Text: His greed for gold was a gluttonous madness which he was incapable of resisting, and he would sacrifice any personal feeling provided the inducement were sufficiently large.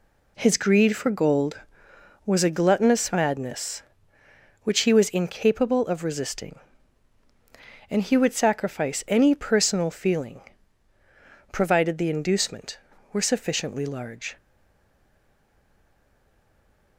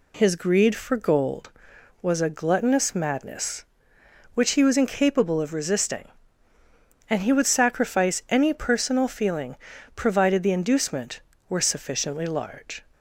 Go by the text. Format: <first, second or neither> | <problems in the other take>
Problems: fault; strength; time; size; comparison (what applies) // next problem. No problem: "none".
second | pauses between "feeling" and "provided"; at 10.4 s; 1.1 s long; also in the second // stays silent after the last word; strong; from 14.3 s on; 2.6 s long